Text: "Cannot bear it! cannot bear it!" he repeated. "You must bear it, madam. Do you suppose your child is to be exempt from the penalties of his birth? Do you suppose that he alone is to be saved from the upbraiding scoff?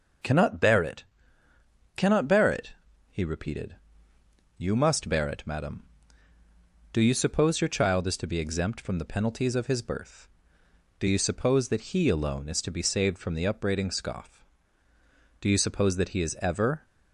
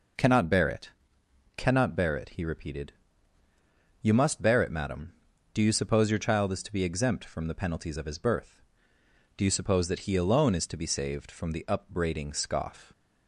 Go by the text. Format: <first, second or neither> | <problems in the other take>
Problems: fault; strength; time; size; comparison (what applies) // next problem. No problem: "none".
second | goes on to say "Do you suppose that he is ever"; from 15.4 s on; 1.4 s long